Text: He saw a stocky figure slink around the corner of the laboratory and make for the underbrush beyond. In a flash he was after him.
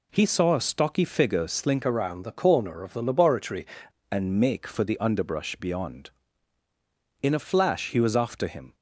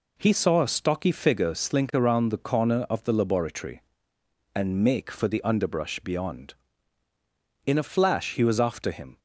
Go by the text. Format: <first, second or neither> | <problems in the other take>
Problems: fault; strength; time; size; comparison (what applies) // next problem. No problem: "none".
second | changes voice from "around" to "laboratory"; from 1.8 to 3.6 s; 1.8 s long